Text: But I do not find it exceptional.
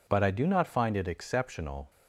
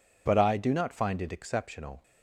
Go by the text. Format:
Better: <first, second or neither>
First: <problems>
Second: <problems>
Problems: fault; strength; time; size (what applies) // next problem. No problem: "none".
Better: neither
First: none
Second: none